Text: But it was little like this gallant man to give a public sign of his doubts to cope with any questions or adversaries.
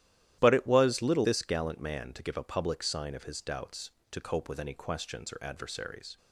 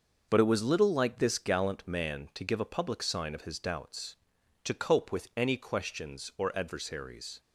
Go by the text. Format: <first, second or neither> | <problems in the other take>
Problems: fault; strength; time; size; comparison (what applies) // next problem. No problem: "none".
second | starts louder than the rest; strong; until 1.4 s; 12.5 dB // skips "like"; at 1.2 s